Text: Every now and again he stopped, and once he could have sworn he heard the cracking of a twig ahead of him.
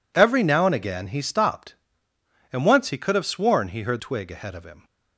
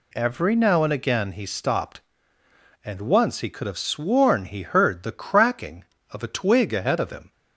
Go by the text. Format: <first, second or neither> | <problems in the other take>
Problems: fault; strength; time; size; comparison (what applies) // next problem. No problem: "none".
second | skips "the cracking of a"; at 3.9 s